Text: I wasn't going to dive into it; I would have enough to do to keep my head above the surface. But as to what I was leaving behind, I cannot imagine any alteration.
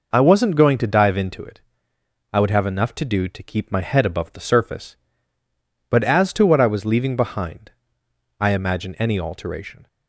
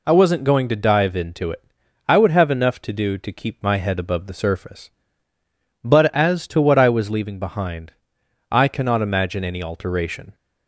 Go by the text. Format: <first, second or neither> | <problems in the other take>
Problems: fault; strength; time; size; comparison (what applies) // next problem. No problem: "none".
second | skips "cannot"; at 8.5 s